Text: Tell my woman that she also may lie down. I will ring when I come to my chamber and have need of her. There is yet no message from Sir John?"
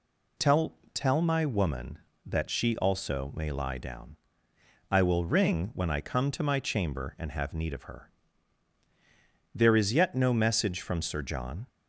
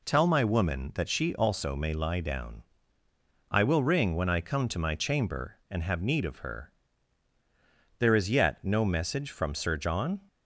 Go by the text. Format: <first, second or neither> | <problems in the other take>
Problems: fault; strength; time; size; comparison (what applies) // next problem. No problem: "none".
second | says "Tell" twice; at 0.9 s